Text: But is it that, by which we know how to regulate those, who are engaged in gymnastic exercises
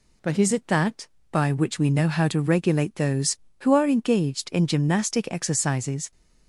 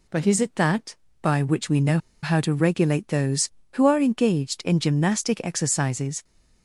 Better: first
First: none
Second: pauses between "know" and "how"; slight; at 1.9 s; 0.25 s long

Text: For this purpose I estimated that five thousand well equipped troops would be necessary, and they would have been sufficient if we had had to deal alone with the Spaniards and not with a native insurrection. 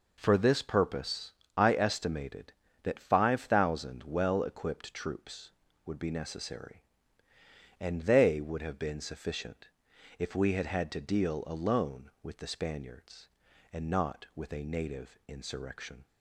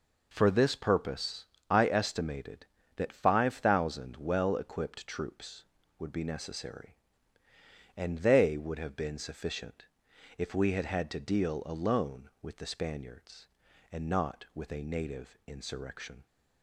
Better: neither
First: pauses between "purpose" and "I"; slight; at 1.3 s; 0.26 s long // pauses between "sufficient" and "if"; noticeable; at 9.6 s; 0.50 s long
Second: pauses between "purpose" and "I"; slight; at 1.4 s; 0.26 s long // pauses between "sufficient" and "if"; noticeable; at 9.8 s; 0.52 s long

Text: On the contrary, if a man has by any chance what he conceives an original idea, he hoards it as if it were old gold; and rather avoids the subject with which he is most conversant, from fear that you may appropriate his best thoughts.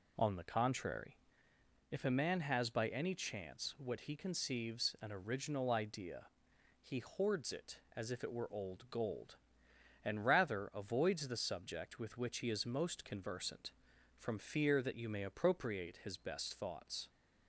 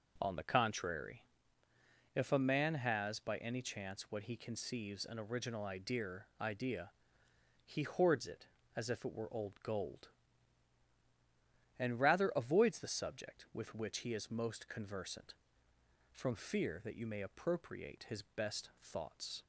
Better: first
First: none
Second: says "idea" twice; at 6.4 s

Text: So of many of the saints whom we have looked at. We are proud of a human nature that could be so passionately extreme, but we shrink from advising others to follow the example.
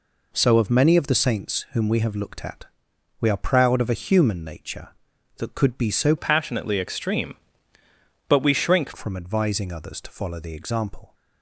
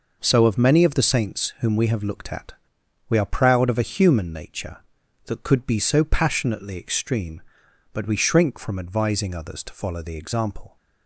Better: second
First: changes voice from "passionately" to "shrink"; from 6.1 to 8.9 s; 2.8 s long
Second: none

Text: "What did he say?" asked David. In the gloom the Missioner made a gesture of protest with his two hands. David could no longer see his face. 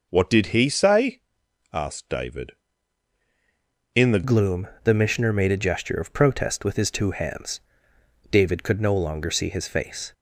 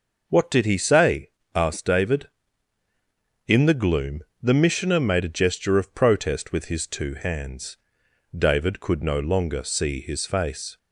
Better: second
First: changes voice at "gloom"; from 4.2 s on; 5.9 s long // pauses between "gloom" and "the"; slight; at 4.6 s; 0.16 s long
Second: pauses between "gloom" and "the"; slight; at 4.2 s; 0.18 s long

